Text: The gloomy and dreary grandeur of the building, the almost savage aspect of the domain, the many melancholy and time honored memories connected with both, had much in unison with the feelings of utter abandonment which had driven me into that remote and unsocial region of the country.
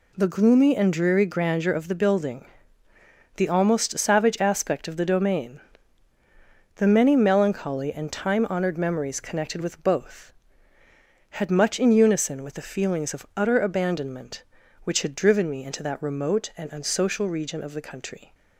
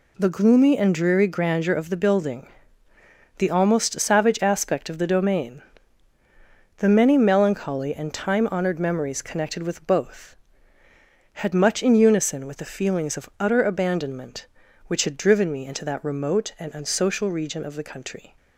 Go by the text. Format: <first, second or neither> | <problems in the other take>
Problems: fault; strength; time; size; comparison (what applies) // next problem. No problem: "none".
neither | none